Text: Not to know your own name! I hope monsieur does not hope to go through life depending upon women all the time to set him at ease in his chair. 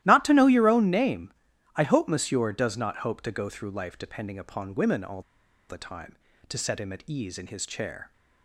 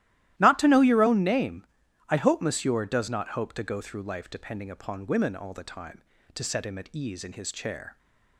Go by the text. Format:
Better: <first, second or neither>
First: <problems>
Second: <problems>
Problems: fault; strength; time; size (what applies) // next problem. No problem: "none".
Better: second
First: starts louder than the rest; strong; until 1.0 s; 14.5 dB // pauses between "all" and "the"; noticeable; at 5.2 s; 0.47 s long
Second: starts louder than the rest; strong; until 1.4 s; 14.5 dB